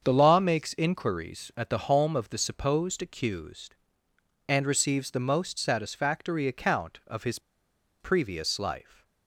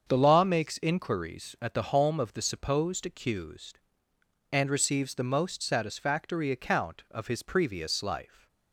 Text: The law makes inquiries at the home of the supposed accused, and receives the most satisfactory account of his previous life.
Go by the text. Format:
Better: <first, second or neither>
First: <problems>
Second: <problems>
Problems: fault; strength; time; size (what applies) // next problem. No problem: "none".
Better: second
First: starts louder than the rest; until 1.0 s; 7 dB // pauses between "his" and "previous"; noticeable; at 7.3 s; 0.60 s long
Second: starts louder than the rest; until 1.0 s; 7 dB